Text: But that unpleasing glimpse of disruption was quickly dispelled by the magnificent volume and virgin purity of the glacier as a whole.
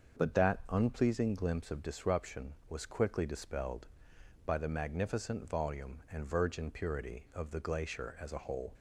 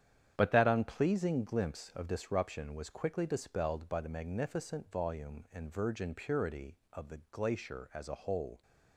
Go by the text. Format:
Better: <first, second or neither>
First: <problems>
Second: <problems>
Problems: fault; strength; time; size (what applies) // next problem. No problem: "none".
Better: first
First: starts louder than the rest; until 1.2 s; 6.5 dB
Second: gets quieter; strong; throughout; 8.5 dB // starts louder than the rest; strong; until 1.3 s; 9.5 dB